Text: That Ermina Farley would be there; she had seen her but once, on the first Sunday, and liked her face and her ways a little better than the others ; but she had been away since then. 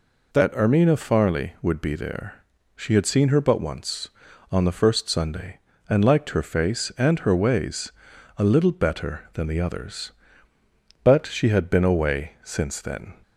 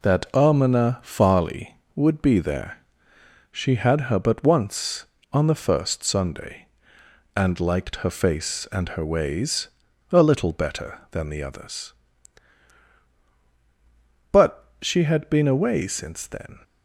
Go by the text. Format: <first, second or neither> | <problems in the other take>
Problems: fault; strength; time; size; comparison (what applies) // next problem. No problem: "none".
first | skips "seen"; at 4.0 s // pauses between "ways" and "a"; at 9.6 s; 0.42 s long; noticeable in the first // pauses between "but" and "she"; slight; at 14.6 s; 0.16 s long